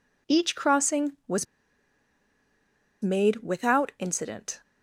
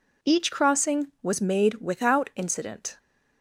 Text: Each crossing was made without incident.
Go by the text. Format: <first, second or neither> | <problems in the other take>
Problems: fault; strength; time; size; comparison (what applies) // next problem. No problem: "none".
second | pauses between "was" and "made"; strong; at 1.4 s; 1.5 s long